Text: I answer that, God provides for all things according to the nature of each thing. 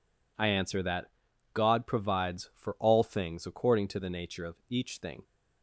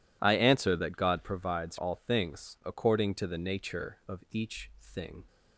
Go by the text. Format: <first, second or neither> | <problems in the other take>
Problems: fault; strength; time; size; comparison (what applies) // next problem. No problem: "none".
first | skips "for"; at 1.7 s